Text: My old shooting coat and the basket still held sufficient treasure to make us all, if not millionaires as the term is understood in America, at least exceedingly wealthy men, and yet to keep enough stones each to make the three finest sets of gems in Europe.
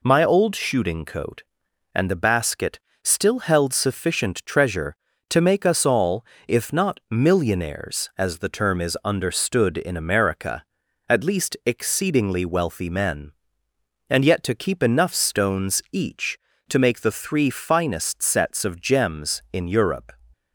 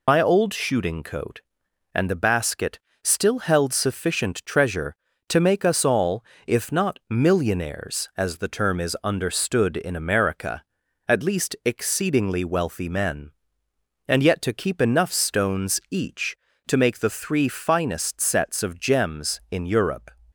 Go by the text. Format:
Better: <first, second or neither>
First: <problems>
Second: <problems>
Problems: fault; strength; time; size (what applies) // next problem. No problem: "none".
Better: first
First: pauses between "basket" and "still"; slight; at 2.7 s; 0.24 s long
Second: loses the start of "My"; at 0.0 s; 70 ms // pauses between "basket" and "still"; slight; at 2.7 s; 0.24 s long